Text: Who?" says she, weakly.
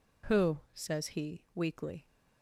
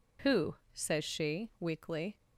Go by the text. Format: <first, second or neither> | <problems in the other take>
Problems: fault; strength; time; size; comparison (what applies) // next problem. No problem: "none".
second | says "he" for "she"; at 1.0 s